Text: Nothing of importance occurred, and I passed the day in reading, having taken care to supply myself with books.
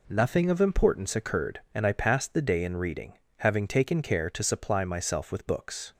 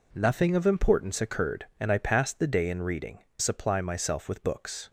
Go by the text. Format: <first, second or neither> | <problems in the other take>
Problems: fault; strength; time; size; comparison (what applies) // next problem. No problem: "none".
first | skips "having taken care to"; at 3.2 s